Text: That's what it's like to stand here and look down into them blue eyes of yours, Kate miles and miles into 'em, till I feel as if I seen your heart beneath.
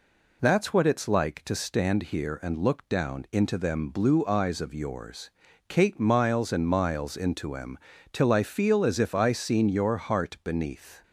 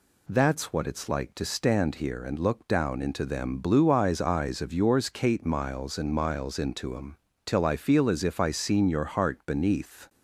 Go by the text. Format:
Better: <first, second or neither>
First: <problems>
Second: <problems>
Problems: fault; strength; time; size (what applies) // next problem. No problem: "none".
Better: first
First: none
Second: says "eyes" twice; at 4.1 s